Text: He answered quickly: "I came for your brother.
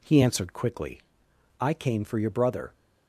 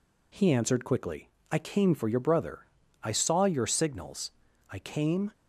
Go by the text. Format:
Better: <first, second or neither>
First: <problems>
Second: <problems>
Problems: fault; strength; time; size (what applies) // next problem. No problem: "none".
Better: first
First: none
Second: goes on to say "I saw your signals I came"; strong; from 3.0 s on; 2.3 s long